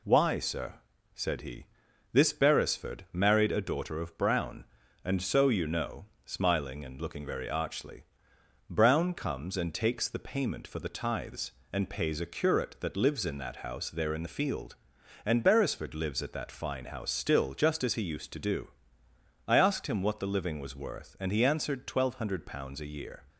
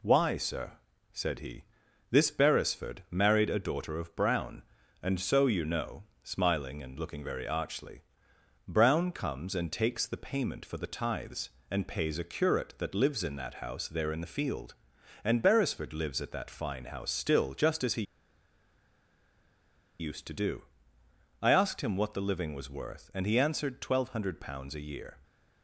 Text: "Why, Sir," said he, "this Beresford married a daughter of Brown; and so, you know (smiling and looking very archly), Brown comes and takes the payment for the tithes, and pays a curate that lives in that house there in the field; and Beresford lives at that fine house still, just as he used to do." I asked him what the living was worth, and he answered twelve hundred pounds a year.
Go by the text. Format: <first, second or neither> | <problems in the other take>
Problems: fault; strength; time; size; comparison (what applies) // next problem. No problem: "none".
first | pauses between "he" and "used"; strong; at 18.0 s; 1.9 s long